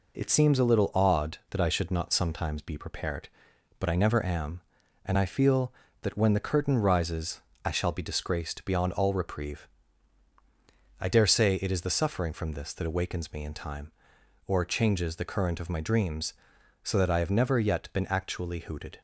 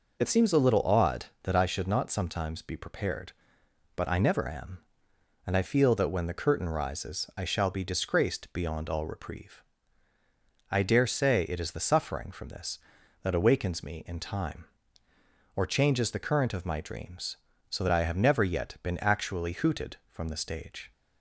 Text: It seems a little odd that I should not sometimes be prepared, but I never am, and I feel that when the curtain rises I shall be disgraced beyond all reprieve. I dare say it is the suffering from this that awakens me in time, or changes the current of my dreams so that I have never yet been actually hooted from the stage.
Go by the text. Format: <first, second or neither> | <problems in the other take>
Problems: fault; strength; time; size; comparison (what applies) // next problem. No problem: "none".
second | pauses between "rises" and "I"; slight; at 7.4 s; 0.24 s long // stops before "from the stage"; at 18.9 s